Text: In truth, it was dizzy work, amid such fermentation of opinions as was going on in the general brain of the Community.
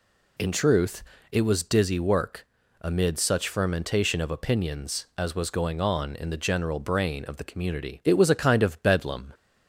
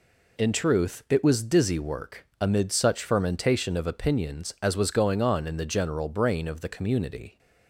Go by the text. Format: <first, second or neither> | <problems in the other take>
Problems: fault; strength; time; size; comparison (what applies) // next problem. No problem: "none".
second | goes on to say "It was a kind of Bedlam"; noticeable; from 8.0 s on; 1.3 s long